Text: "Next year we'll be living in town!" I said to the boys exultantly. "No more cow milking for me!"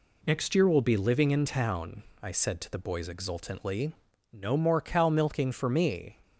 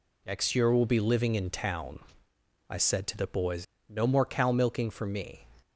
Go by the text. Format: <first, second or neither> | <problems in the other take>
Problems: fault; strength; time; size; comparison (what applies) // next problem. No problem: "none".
first | skips "exultantly"; at 3.7 s